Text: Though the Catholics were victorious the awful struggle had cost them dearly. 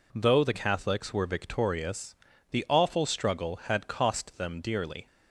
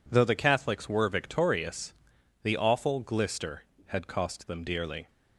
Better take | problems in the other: first | pauses between "victorious" and "the"; noticeable; at 1.9 s; 0.50 s long; slight in the first // says "glister" for "struggle"; at 3.0 s

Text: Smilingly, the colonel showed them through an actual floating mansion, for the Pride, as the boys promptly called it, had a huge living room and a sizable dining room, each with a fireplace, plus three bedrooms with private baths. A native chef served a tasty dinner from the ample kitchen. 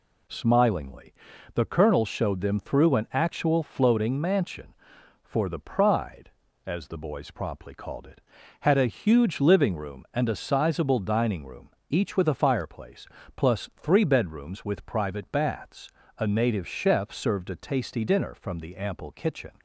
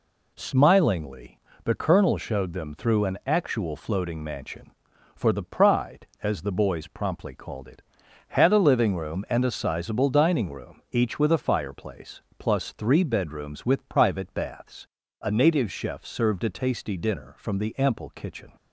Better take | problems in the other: first | skips "huge"; at 8.5 s

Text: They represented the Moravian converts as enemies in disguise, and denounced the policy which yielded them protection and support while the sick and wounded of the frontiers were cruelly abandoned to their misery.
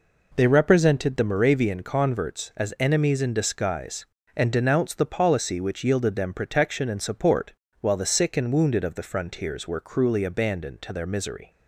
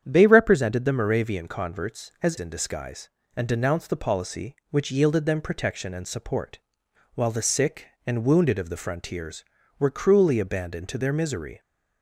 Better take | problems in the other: first | starts louder than the rest; strong; until 1.0 s; 8.5 dB // skips "enemies"; at 2.3 s // pauses between "support" and "while"; noticeable; at 6.5 s; 0.56 s long; slight in the first

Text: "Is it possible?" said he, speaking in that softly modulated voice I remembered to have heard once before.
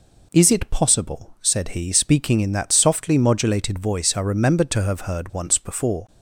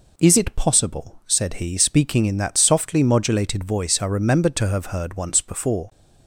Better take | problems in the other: neither | none

